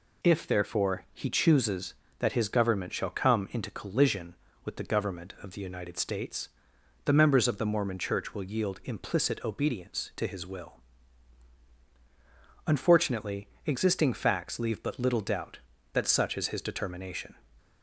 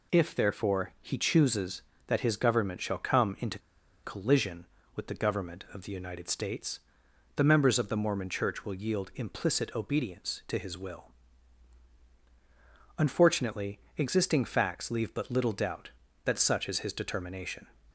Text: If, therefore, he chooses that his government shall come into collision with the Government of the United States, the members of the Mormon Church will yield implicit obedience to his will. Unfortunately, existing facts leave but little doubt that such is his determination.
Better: first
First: none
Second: pauses between "into" and "collision"; at 3.5 s; 0.44 s long

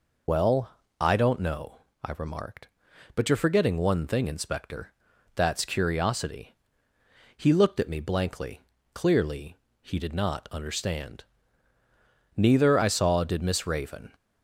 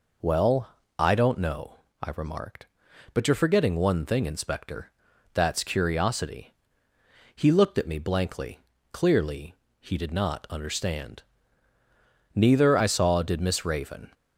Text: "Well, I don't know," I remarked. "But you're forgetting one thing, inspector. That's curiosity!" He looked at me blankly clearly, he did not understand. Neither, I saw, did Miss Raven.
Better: second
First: loses the start of "Well"; at 0.2 s; 55 ms // pauses between "blankly" and "clearly"; slight; at 8.6 s; 0.32 s long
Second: pauses between "blankly" and "clearly"; slight; at 8.5 s; 0.32 s long

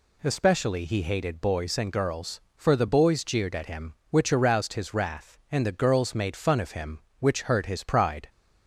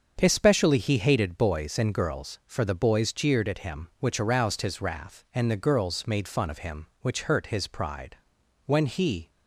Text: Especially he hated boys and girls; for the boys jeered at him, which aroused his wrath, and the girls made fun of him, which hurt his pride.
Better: first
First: none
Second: starts louder than the rest; until 1.2 s; 7 dB // goes on to say "When he"; noticeable; from 8.6 s on; 0.64 s long

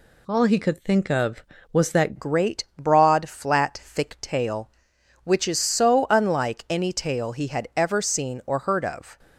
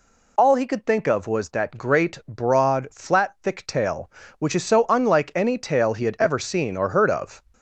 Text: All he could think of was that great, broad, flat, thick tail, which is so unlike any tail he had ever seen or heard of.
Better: second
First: changes voice at "great"; from 2.1 s on; 7.0 s long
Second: none

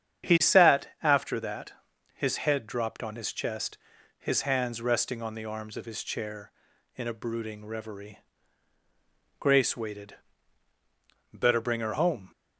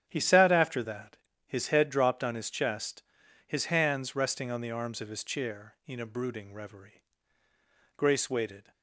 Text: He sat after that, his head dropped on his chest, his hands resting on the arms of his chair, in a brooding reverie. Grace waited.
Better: second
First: starts louder than the rest; strong; until 1.4 s; 8.5 dB // goes on to say "Better bring her home"; noticeable; from 11.3 s on; 0.98 s long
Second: starts louder than the rest; strong; until 1.1 s; 9.5 dB

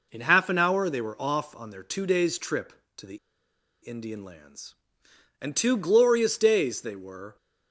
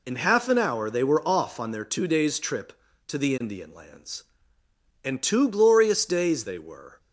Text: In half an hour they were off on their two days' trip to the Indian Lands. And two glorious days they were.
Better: second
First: pauses between "the" and "Indian"; noticeable; at 3.1 s; 0.65 s long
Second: none

